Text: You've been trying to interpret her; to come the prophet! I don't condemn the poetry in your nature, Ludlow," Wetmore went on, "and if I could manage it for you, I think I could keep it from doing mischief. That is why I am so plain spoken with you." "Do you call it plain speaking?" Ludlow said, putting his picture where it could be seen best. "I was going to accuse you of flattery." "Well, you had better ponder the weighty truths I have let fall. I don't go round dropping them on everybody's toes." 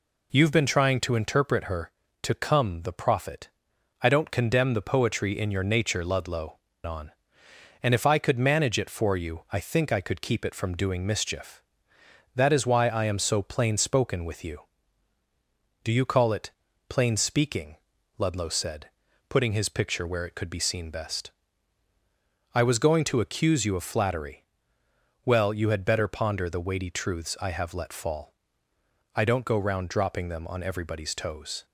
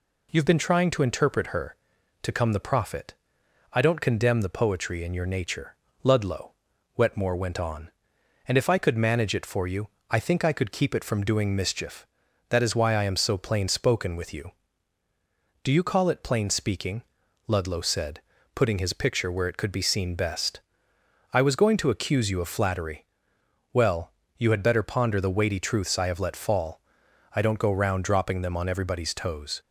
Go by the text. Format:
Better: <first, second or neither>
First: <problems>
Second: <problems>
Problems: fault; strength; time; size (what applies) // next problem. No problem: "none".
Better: second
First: skips "Wetmore went"; at 6.7 s // pauses between "it" and "plain"; at 16.4 s; 0.40 s long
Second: none